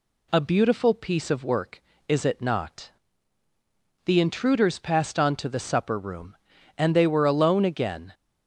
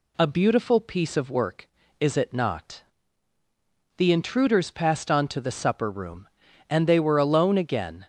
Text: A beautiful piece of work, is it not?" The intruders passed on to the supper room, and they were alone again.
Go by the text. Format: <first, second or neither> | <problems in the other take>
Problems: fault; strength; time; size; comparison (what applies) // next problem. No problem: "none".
neither | none